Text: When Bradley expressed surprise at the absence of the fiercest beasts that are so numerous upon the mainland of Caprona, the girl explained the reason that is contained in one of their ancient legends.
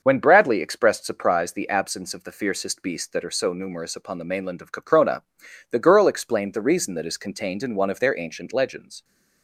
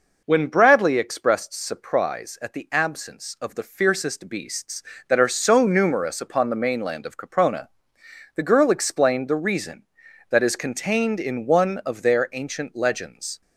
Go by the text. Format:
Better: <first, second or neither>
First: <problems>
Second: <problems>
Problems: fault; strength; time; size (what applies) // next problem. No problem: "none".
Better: second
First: starts louder than the rest; until 1.0 s; 6.5 dB // skips "at"; at 1.5 s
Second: none